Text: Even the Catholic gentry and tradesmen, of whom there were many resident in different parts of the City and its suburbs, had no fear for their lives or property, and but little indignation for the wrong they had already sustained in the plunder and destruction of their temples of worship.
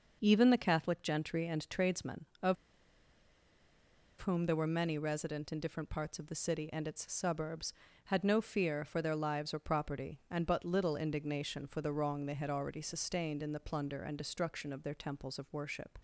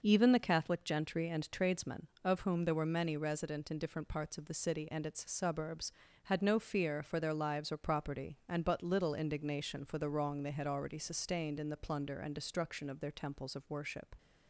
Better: second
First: starts louder than the rest; noticeable; until 1.2 s; 6 dB // pauses between "of" and "whom"; strong; at 2.5 s; 1.6 s long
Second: starts louder than the rest; noticeable; until 1.0 s; 6 dB

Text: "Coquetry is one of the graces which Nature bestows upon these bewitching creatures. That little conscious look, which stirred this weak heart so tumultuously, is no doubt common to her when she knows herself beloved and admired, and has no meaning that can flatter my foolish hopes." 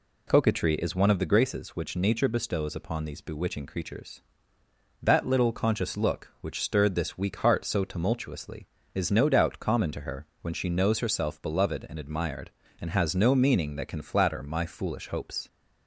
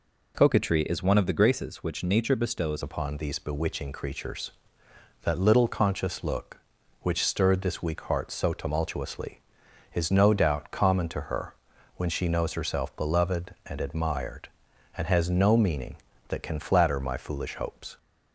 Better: first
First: none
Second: changes voice at "upon"; from 2.8 s on; 15.1 s long // pauses between "her" and "when"; at 11.5 s; 0.42 s long

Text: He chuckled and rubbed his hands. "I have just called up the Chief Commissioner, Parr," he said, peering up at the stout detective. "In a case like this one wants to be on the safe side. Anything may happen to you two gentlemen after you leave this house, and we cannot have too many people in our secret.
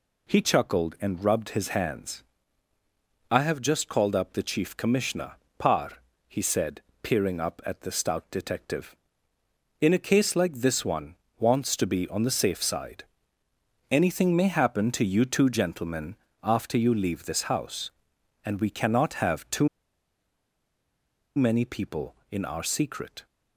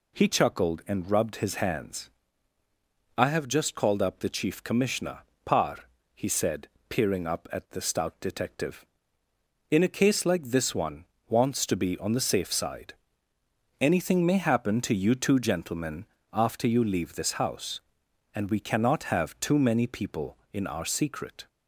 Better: second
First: pauses between "one" and "wants"; slight; at 11.1 s; 0.22 s long // pauses between "gentlemen" and "after"; slight; at 16.1 s; 0.28 s long // pauses between "too" and "many"; strong; at 19.6 s; 1.6 s long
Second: pauses between "one" and "wants"; slight; at 11.0 s; 0.22 s long // pauses between "gentlemen" and "after"; slight; at 16.0 s; 0.28 s long

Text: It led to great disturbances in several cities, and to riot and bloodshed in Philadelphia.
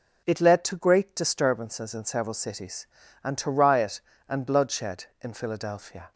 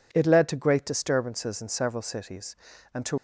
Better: first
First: none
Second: stops before "riot and bloodshed in Philadelphia"; at 3.1 s

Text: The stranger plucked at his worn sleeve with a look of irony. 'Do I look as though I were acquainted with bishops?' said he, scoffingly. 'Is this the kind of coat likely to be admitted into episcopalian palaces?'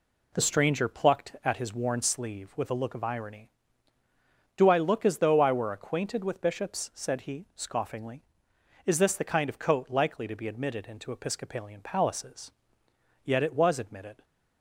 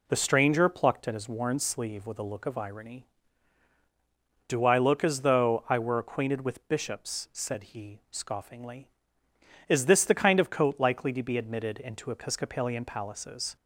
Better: second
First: goes on to say "Yet it was admitted"; noticeable; from 13.2 s on; 1.0 s long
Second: none

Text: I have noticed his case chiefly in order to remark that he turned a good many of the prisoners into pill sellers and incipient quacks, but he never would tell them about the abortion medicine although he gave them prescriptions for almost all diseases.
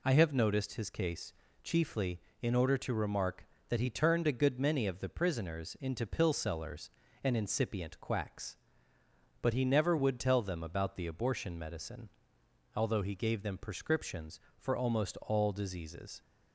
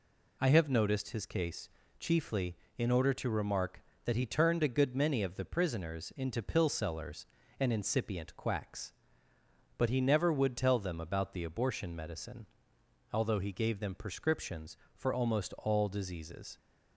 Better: neither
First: pauses between "case" and "chiefly"; slight; at 1.3 s; 0.32 s long // pauses between "medicine" and "although"; noticeable; at 12.0 s; 0.66 s long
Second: pauses between "case" and "chiefly"; slight; at 1.6 s; 0.32 s long // pauses between "medicine" and "although"; noticeable; at 12.4 s; 0.66 s long

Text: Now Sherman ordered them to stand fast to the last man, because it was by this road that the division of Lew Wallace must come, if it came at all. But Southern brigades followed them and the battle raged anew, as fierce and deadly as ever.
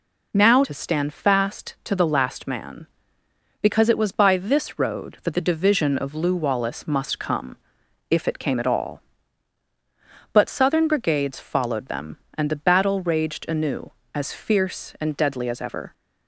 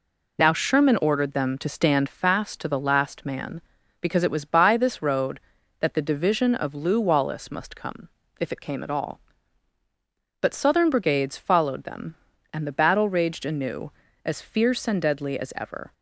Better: second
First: skips "Sherman ordered them"; at 0.6 s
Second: none

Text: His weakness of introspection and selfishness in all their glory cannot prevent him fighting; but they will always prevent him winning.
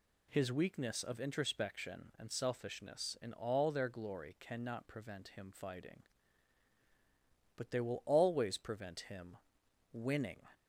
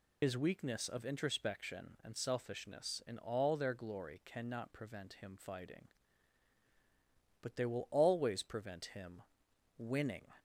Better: first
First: pauses between "him" and "winning"; noticeable; at 9.3 s; 0.54 s long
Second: loses the start of "His"; at 0.2 s; 75 ms // pauses between "him" and "winning"; noticeable; at 9.2 s; 0.54 s long

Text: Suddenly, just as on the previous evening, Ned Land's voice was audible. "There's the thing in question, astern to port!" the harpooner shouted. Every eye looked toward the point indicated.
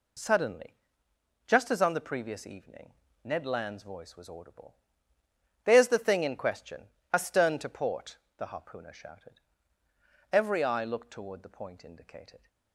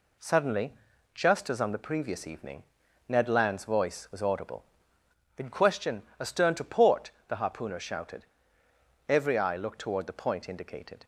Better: first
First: none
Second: skips "There's the thing"; at 5.0 s

